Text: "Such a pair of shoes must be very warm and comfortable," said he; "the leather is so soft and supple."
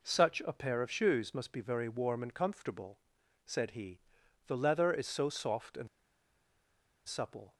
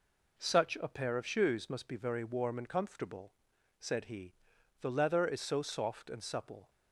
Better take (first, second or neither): second